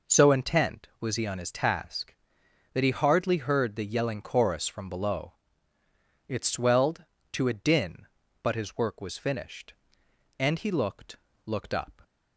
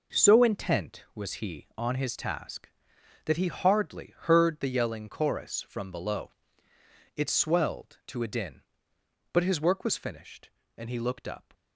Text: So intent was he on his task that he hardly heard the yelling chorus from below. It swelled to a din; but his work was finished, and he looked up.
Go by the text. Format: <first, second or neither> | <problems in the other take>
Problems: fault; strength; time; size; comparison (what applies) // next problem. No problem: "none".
second | says "looked" twice; at 11.4 s